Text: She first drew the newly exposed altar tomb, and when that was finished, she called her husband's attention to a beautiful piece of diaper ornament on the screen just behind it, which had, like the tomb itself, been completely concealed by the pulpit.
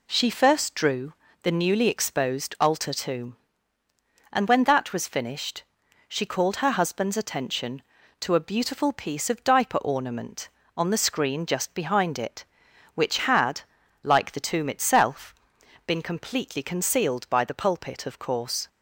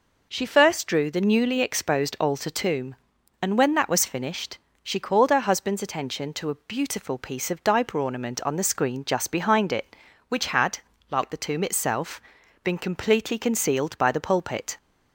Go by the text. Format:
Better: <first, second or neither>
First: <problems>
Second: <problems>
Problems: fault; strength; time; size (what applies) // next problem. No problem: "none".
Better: second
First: pauses between "drew" and "the"; slight; at 1.1 s; 0.28 s long // goes on to say "Of course"; noticeable; from 18.0 s on; 0.62 s long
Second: none